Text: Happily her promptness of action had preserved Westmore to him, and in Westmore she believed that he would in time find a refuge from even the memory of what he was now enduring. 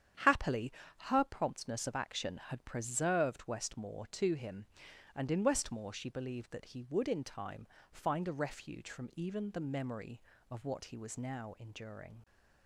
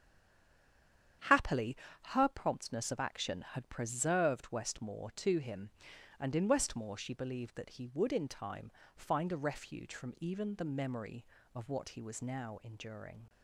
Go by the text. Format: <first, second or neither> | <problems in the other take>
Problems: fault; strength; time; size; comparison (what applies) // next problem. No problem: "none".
first | stays silent before the first word; noticeable; until 1.2 s; 1.2 s long // starts louder than the rest; strong; until 2.5 s; 9 dB; strong in the first // pauses between "Happily" and "her"; slight; at 1.7 s; 0.34 s long; slight in the first // pauses between "time" and "find"; slight; at 8.7 s; 0.24 s long; slight in the first